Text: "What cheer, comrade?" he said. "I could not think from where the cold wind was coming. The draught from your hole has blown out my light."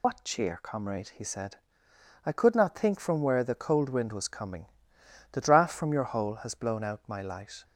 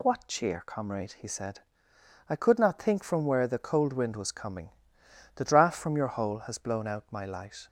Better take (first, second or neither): second